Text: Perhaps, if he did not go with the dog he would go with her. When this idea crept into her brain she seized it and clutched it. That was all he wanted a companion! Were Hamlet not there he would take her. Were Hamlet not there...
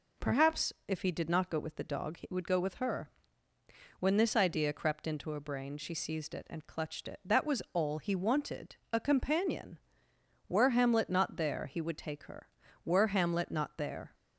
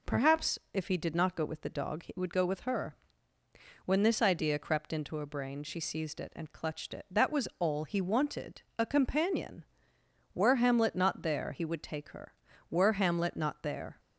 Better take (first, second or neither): neither